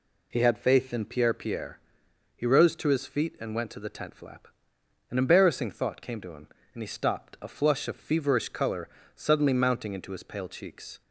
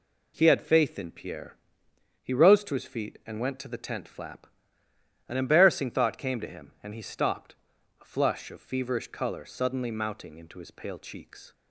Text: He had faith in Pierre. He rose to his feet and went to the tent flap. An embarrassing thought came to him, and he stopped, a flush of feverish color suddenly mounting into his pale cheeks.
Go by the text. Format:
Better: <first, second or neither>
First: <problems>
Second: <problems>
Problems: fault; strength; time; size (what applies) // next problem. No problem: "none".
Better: second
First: says "Pierre" twice; at 1.3 s // pauses between "color" and "suddenly"; slight; at 8.8 s; 0.26 s long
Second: none